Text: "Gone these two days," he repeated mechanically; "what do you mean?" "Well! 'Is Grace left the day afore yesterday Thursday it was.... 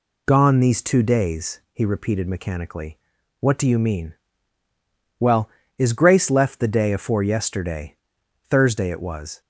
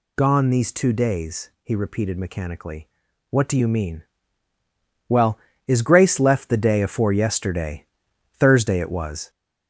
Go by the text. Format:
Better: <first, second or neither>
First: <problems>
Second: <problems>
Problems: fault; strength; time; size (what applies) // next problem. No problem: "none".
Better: first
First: pauses between "yesterday" and "Thursday"; noticeable; at 7.9 s; 0.56 s long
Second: gets louder; noticeable; throughout; 5 dB // pauses between "yesterday" and "Thursday"; noticeable; at 7.8 s; 0.56 s long